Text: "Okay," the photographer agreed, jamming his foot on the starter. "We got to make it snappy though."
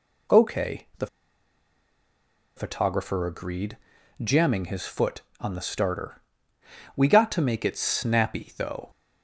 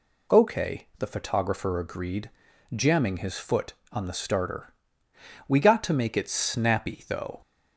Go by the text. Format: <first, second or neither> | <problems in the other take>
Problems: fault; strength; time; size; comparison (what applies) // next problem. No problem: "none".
second | pauses between "the" and "photographer"; strong; at 1.0 s; 1.4 s long